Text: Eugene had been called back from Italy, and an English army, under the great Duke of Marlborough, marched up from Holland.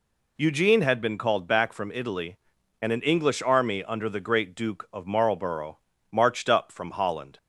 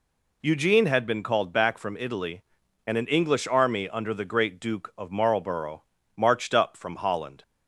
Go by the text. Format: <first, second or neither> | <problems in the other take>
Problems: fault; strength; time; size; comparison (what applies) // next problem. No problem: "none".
neither | none